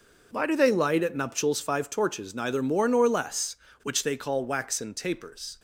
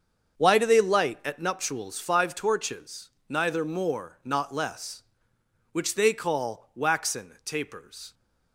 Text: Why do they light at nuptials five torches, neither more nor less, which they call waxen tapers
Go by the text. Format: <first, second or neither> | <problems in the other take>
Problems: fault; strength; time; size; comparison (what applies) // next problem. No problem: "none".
first | starts louder than the rest; until 1.4 s; 7 dB // says "not" for "nor"; at 4.2 s